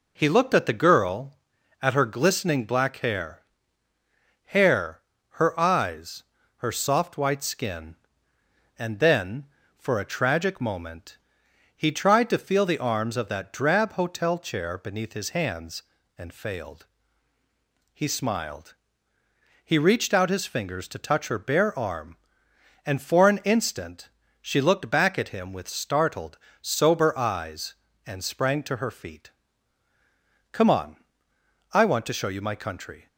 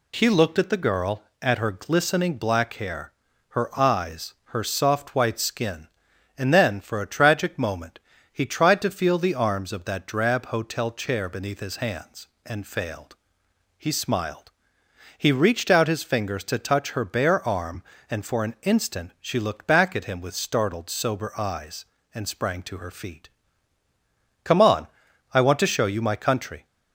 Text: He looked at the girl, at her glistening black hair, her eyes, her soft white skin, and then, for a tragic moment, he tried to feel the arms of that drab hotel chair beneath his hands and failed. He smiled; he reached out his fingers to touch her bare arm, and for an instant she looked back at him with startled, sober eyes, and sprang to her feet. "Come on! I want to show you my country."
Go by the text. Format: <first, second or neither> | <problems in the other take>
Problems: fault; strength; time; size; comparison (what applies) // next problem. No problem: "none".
second | says "hair" twice; at 4.4 s // pauses between "instant" and "she"; slight; at 24.0 s; 0.34 s long